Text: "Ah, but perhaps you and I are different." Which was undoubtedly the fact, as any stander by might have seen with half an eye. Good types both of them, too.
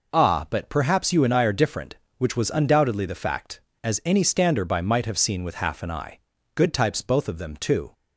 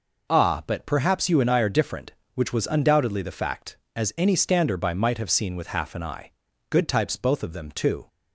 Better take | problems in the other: neither | none

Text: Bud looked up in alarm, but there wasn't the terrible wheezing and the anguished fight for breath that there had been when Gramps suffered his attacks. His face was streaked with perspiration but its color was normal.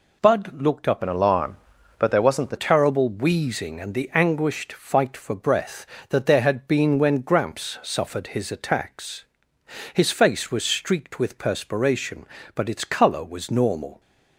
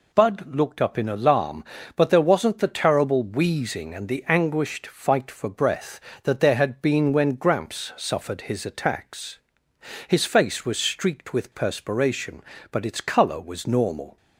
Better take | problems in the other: second | changes voice from "in" to "the"; from 1.0 to 2.5 s; 1.5 s long

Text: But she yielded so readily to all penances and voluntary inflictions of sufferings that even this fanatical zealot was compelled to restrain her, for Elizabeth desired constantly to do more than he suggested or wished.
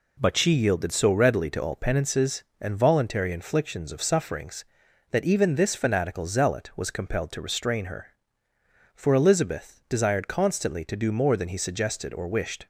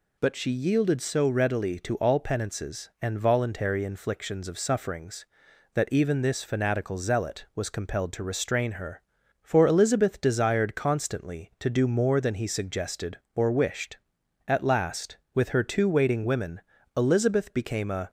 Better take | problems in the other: first | goes on to say "At last with her two waiting women Elizabeth became a"; strong; from 14.4 s on; 3.6 s long

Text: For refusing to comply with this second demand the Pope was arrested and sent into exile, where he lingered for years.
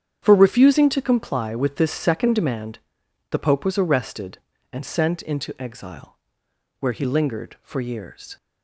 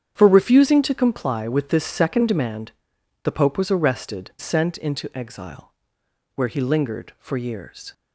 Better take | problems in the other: first | starts louder than the rest; strong; until 1.1 s; 8.5 dB; strong in the first // pauses between "demand" and "the"; noticeable; at 2.7 s; 0.54 s long; noticeable in the first // skips "and"; at 4.3 s

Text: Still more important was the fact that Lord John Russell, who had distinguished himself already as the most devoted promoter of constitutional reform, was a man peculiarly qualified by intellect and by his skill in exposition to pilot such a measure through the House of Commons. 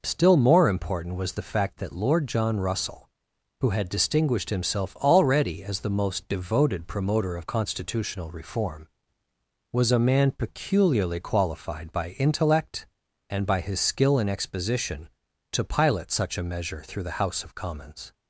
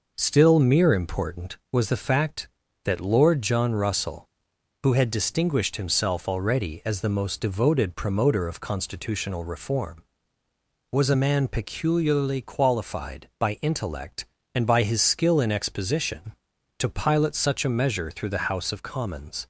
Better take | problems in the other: first | says "mere" for "more"; at 0.5 s

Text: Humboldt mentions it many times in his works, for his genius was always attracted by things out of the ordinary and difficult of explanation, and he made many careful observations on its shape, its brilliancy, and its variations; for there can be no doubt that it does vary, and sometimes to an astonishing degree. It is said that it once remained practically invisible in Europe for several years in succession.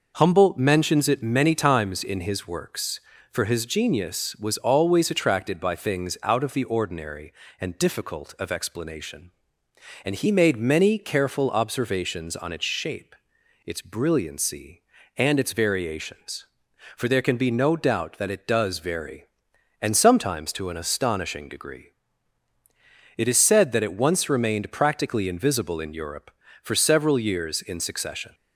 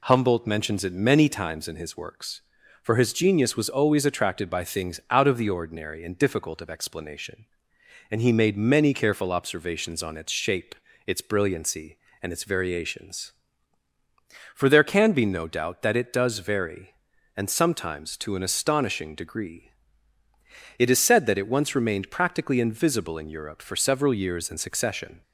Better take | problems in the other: neither | none

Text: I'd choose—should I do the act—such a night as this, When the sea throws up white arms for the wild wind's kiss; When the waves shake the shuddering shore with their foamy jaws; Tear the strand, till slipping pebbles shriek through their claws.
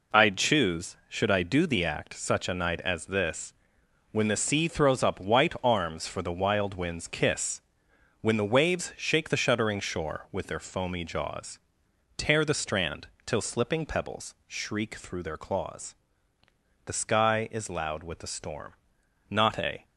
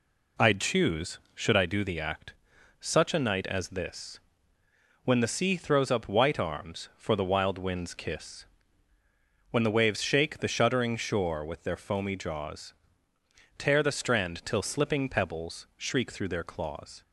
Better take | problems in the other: second | goes on to say "The sky is loud with the storm not a"; strong; from 16.8 s on; 2.9 s long

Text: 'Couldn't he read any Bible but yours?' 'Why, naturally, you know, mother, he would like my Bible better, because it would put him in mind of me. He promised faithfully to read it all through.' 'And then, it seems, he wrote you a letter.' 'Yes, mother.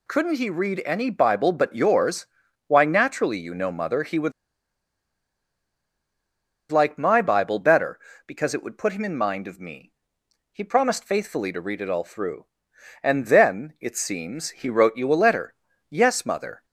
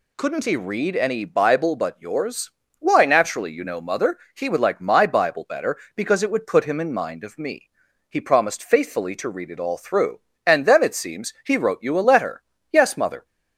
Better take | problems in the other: second | pauses between "would" and "like"; strong; at 4.3 s; 2.3 s long

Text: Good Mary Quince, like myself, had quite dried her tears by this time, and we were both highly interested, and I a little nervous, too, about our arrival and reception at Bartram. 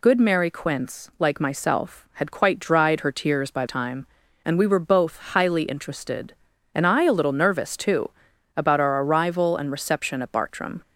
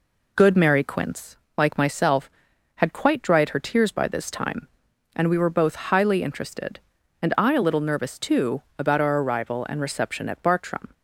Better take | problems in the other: second | skips "this"; at 3.6 s

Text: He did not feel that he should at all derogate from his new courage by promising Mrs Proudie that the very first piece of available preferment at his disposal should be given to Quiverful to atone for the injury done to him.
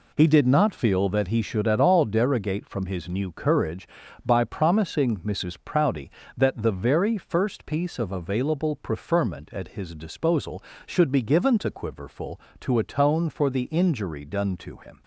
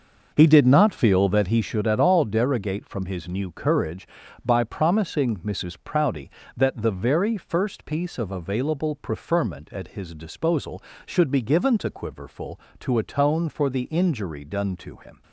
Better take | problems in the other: first | starts louder than the rest; noticeable; until 1.8 s; 6 dB

